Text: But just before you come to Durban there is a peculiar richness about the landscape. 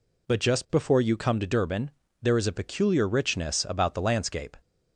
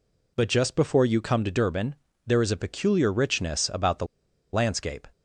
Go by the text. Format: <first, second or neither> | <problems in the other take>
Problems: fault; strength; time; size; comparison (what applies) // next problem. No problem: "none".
first | pauses between "Durban" and "there"; slight; at 1.9 s; 0.30 s long; slight in the first // pauses between "the" and "landscape"; noticeable; at 4.0 s; 0.47 s long